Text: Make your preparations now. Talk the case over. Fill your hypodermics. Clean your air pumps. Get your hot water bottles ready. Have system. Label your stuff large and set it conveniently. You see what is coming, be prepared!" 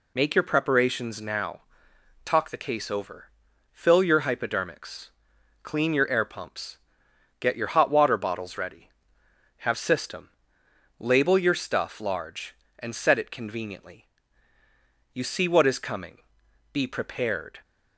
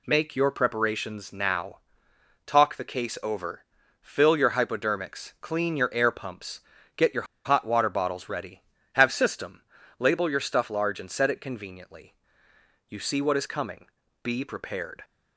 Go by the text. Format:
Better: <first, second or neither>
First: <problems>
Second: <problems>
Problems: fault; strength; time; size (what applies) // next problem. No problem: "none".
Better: first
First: none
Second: pauses between "your" and "hot"; slight; at 7.2 s; 0.21 s long